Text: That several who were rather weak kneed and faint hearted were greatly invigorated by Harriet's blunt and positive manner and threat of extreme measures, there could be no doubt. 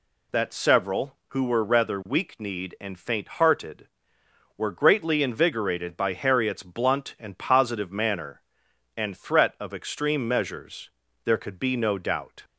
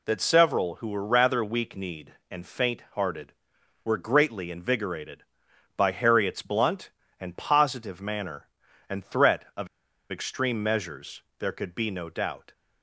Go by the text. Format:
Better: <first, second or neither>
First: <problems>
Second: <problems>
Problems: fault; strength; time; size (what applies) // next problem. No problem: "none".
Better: first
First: none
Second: pauses between "of" and "extreme"; at 9.6 s; 0.44 s long